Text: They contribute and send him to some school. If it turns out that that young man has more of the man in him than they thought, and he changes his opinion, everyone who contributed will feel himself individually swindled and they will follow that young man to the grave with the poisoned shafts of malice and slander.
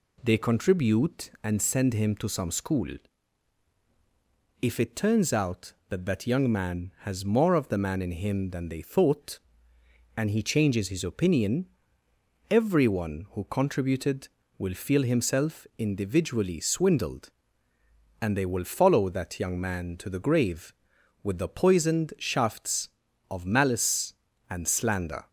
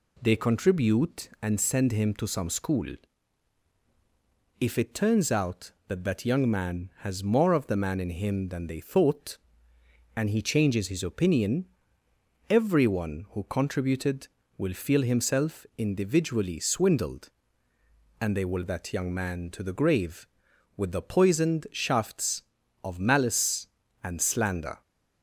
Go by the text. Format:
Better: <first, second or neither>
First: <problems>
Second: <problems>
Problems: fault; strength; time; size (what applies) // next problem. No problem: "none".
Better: first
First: none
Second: skips "follow"; at 18.6 s